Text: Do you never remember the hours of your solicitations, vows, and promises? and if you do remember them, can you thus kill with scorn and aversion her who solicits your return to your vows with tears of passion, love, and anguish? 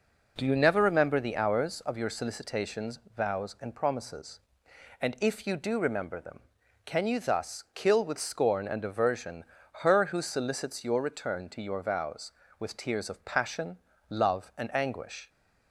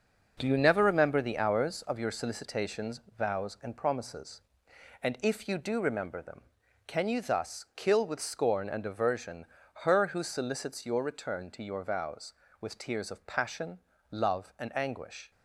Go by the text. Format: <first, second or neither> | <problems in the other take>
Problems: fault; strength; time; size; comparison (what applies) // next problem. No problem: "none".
first | gets quieter; strong; throughout; 8 dB // pauses between "aversion" and "her"; at 9.4 s; 0.40 s long; also in the first